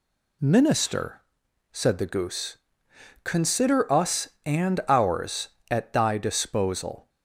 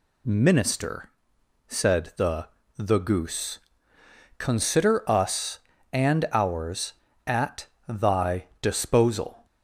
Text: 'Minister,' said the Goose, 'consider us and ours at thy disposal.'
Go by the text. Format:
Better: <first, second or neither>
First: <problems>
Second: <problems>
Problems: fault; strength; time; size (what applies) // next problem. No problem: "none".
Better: first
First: none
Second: says "the" twice; at 2.7 s // pauses between "at" and "thy"; slight; at 7.6 s; 0.20 s long // pauses between "thy" and "disposal"; slight; at 8.4 s; 0.18 s long